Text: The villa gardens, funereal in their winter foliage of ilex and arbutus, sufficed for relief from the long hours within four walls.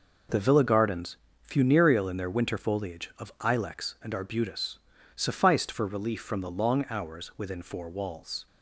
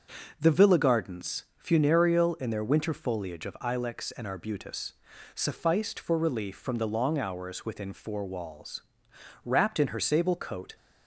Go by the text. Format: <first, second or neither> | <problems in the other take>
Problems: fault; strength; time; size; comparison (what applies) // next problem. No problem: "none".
first | goes on to say "Wrapped in her sable coat"; from 9.4 s on; 1.3 s long